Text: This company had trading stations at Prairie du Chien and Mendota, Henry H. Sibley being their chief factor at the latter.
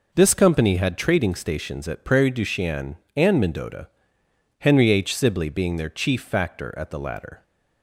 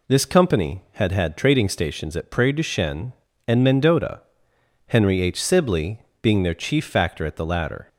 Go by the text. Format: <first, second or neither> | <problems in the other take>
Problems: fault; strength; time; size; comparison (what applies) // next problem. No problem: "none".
first | says "had" twice; at 1.1 s // pauses between "Sibley" and "being"; slight; at 5.9 s; 0.20 s long